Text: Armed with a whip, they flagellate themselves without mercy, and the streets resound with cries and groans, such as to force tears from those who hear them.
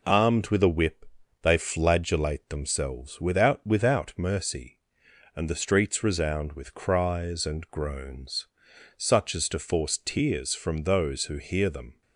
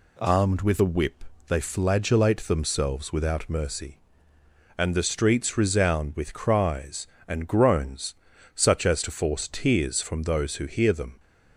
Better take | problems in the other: second | says "without" twice; at 3.6 s

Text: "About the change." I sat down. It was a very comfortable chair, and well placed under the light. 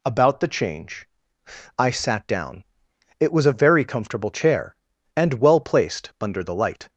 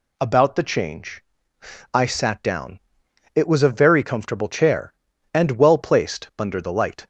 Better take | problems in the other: neither | none

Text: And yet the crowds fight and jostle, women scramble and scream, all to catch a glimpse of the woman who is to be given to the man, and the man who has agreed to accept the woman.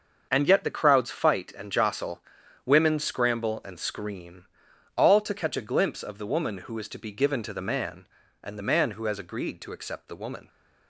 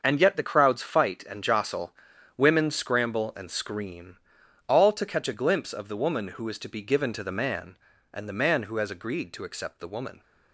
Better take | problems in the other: neither | starts louder than the rest; the same in both

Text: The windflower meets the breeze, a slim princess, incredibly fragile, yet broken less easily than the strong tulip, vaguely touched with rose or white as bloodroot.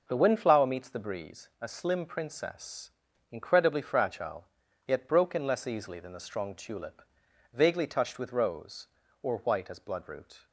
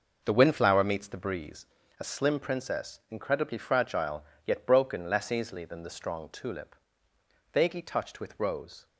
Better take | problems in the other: first | stops before "or white as bloodroot"; at 8.8 s

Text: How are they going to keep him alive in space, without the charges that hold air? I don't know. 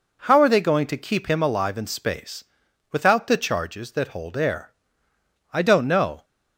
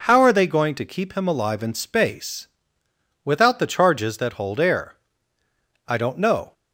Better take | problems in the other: neither | none

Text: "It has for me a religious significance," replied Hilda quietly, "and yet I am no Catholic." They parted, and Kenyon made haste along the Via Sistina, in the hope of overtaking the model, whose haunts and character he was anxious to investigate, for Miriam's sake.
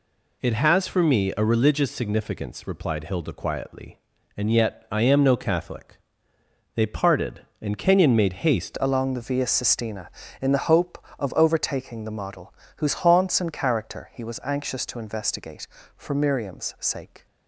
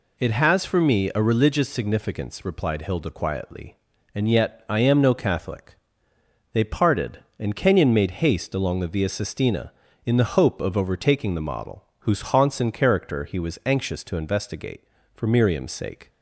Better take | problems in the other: second | changes voice at "along"; from 8.7 s on; 8.5 s long

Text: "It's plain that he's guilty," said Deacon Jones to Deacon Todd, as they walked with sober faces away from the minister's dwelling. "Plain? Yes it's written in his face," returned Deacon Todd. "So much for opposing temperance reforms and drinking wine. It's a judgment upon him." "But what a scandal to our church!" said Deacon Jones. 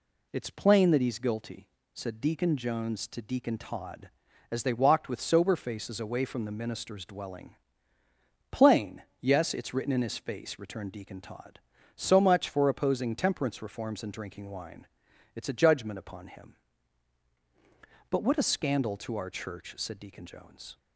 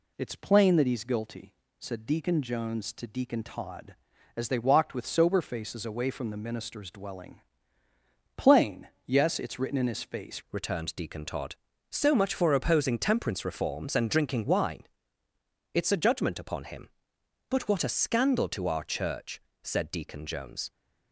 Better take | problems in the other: first | changes voice at "returned"; from 10.5 s on; 10.2 s long

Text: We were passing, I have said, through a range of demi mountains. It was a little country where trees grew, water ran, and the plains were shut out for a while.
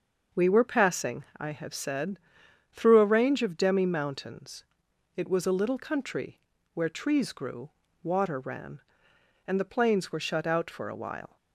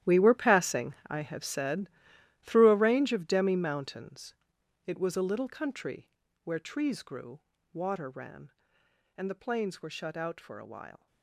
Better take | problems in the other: first | gets quieter; strong; throughout; 15 dB // starts louder than the rest; strong; until 1.1 s; 12 dB; noticeable in the first // pauses between "country" and "where"; slight; at 6.0 s; 0.32 s long; slight in the first

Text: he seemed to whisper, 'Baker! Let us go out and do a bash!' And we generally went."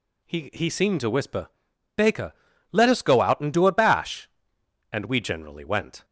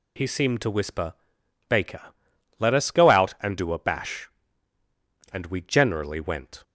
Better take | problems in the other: second | says "he" twice; at 0.5 s

